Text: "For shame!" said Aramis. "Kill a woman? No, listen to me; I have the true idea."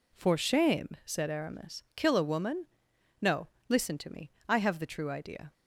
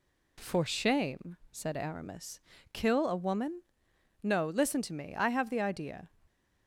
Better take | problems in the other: first | skips "true"; at 5.5 s

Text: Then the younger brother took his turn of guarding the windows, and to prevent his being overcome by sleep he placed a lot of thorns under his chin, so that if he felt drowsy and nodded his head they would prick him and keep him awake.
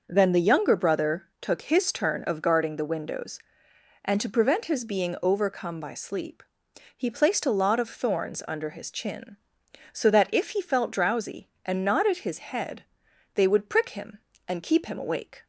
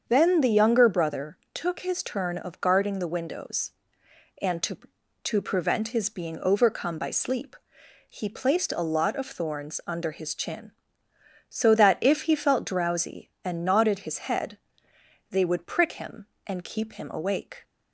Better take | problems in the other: first | starts louder than the rest; strong; until 1.0 s; 7 dB // pauses between "brother" and "took"; slight; at 1.3 s; 0.16 s long // says "to" twice; at 5.2 s // pauses between "sleep" and "he"; noticeable; at 7.5 s; 0.54 s long; noticeable in the first // pauses between "head" and "they"; noticeable; at 14.5 s; 0.72 s long; noticeable in the first

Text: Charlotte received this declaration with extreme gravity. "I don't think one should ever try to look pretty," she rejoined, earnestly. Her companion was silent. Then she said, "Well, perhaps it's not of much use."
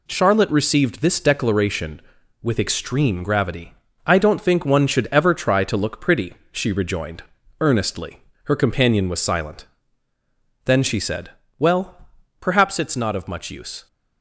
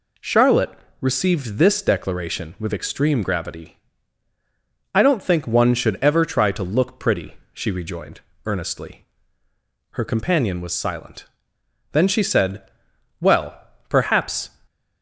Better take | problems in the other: first | pauses between "Charlotte" and "received"; slight; at 0.7 s; 0.28 s long // stops before "it's not of much use"; at 14.6 s

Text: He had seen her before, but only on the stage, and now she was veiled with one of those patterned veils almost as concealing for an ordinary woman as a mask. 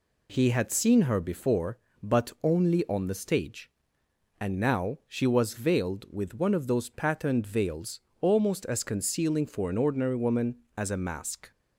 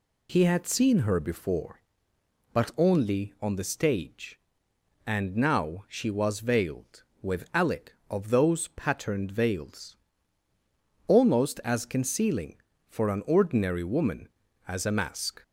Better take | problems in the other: first | says "alec" for "one"; at 7.5 s // pauses between "veils" and "almost"; at 9.9 s; 1.1 s long; slight in the first

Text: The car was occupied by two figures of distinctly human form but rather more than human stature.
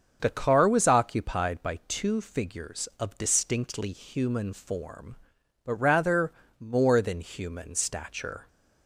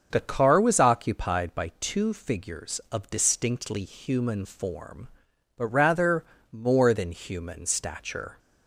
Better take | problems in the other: neither | starts louder than the rest; the same in both // pauses between "rather" and "more"; slight; the same in both

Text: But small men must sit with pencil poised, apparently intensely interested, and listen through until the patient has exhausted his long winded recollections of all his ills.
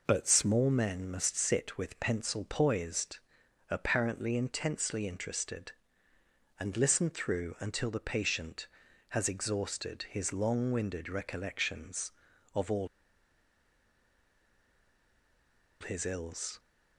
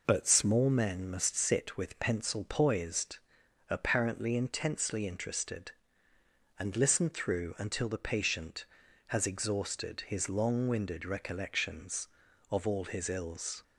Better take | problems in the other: second | pauses between "all" and "his"; strong; at 12.8 s; 2.9 s long

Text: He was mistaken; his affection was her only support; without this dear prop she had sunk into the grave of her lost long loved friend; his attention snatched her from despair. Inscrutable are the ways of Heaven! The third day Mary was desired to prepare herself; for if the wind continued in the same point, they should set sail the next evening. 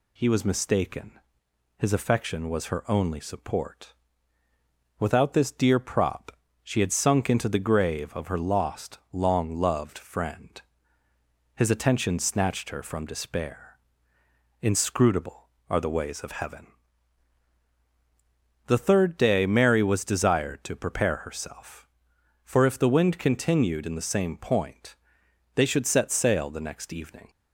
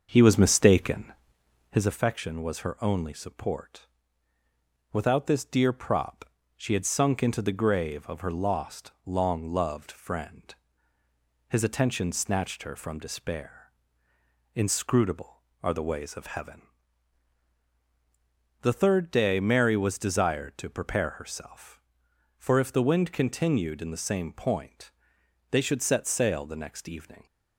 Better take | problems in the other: first | starts louder than the rest; until 1.9 s; 6.5 dB // pauses between "prop" and "she"; slight; at 6.2 s; 0.32 s long; slight in the first

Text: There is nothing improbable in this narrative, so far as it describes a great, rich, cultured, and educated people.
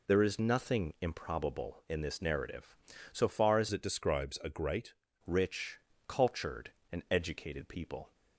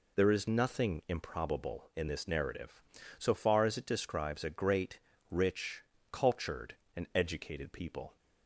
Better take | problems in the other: second | changes voice from "it" to "great"; from 3.7 to 4.9 s; 1.2 s long

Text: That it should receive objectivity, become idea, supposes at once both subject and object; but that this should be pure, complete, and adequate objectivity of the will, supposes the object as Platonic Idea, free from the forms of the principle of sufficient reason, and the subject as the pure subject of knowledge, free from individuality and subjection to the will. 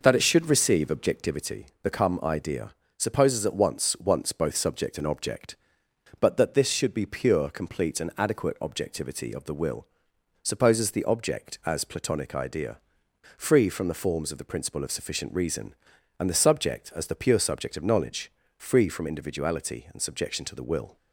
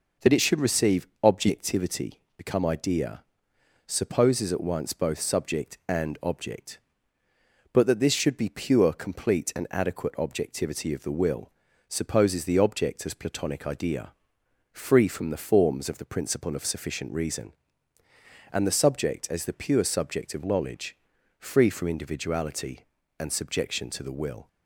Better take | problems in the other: second | says "once" twice; at 3.9 s

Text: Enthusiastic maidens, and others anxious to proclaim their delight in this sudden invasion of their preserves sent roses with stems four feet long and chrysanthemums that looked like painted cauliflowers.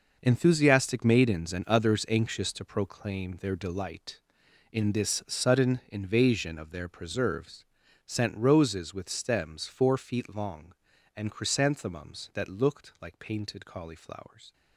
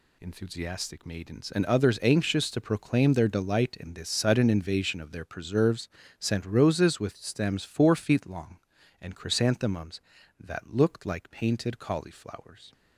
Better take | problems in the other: second | gets quieter; strong; throughout; 11.5 dB // pauses between "preserves" and "sent"; at 7.6 s; 0.40 s long; slight in the second

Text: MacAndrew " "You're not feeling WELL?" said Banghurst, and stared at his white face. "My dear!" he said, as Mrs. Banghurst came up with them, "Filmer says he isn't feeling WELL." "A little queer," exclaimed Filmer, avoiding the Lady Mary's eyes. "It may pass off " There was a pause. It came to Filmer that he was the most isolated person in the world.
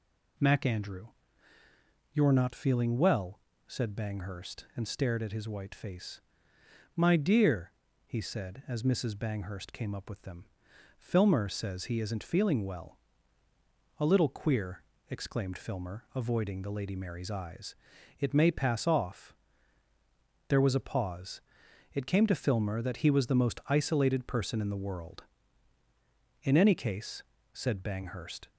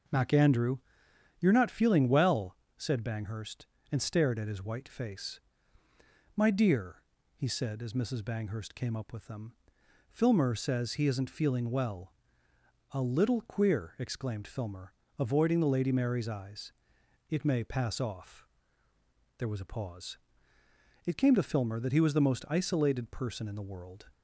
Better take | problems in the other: second | goes on to say "In any case said Banghurst"; strong; from 26.4 s on; 2.0 s long

